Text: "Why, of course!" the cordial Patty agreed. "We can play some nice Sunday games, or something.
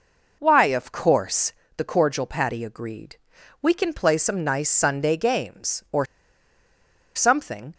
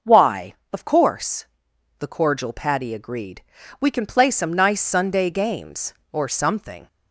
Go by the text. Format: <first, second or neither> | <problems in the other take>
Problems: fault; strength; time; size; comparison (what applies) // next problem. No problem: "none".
second | pauses between "or" and "something"; at 6.0 s; 1.1 s long